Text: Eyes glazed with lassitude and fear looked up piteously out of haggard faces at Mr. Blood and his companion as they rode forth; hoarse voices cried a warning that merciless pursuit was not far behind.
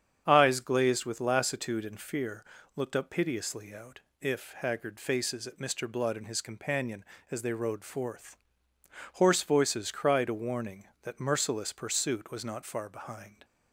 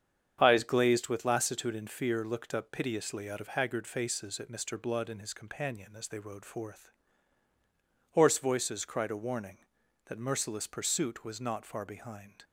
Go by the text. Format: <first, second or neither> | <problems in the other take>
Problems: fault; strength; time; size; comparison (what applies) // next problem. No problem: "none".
second | starts louder than the rest; strong; until 1.2 s; 8 dB; strong in the second // pauses between "fear" and "looked"; slight; at 2.4 s; 0.32 s long // says "if" for "of"; at 4.2 s